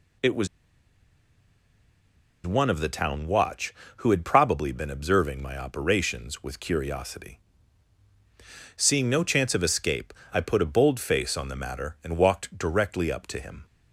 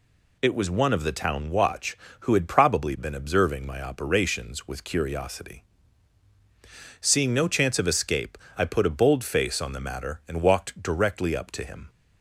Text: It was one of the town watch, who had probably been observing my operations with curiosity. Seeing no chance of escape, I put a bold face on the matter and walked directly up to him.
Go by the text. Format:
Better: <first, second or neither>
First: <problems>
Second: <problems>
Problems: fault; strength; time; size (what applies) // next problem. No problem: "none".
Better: second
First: pauses between "was" and "one"; strong; at 0.4 s; 1.9 s long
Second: none